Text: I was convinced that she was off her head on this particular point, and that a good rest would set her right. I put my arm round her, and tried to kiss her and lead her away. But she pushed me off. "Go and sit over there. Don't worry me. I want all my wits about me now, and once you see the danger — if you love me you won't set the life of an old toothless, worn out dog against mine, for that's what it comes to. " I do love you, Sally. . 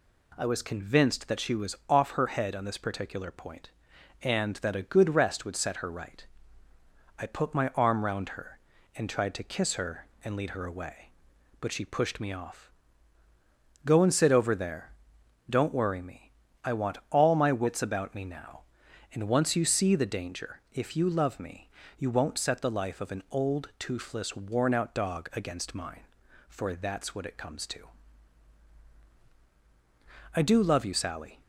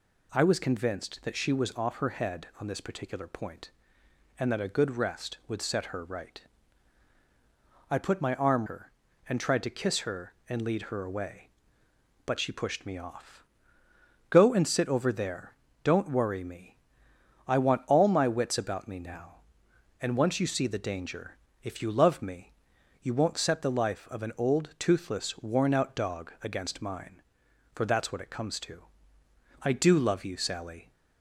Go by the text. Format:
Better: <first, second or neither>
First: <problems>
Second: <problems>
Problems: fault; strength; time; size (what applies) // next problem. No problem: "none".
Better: first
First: pauses between "me" and "you"; slight; at 21.6 s; 0.30 s long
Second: skips "round"; at 8.6 s // pauses between "me" and "you"; noticeable; at 22.5 s; 0.50 s long